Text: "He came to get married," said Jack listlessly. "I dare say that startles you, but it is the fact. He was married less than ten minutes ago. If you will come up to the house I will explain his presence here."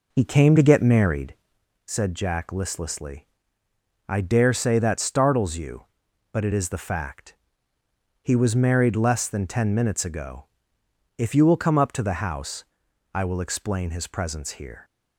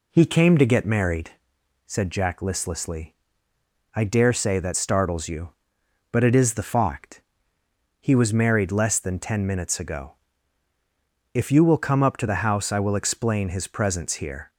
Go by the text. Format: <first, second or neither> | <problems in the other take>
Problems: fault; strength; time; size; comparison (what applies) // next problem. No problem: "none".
second | starts louder than the rest; noticeable; until 1.6 s; 4 dB // pauses between "house" and "I"; noticeable; at 12.6 s; 0.50 s long